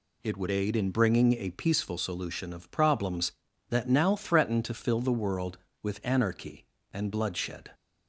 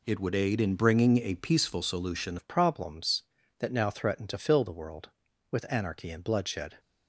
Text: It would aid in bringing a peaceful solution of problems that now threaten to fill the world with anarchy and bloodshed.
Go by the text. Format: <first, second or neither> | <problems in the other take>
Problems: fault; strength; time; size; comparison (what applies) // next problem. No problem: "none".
first | changes voice at "of"; from 2.3 s on; 4.4 s long